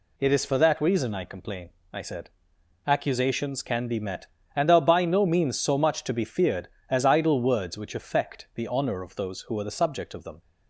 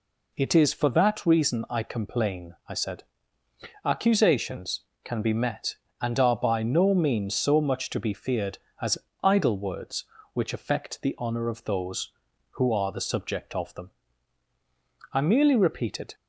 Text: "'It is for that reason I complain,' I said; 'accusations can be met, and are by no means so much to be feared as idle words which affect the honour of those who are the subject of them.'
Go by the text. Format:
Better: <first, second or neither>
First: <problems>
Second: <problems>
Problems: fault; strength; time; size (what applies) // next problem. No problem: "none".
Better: first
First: none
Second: pauses between "as" and "idle"; slight; at 8.9 s; 0.26 s long // goes on to say "I merely repeated"; noticeable; from 15.1 s on; 1.0 s long